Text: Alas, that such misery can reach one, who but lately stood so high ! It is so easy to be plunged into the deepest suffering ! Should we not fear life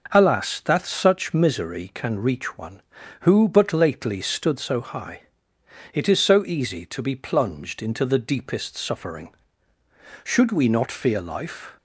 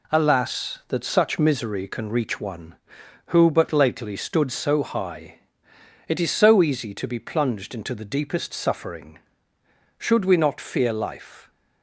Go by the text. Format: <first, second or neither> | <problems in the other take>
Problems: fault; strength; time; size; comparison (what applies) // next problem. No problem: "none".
neither | none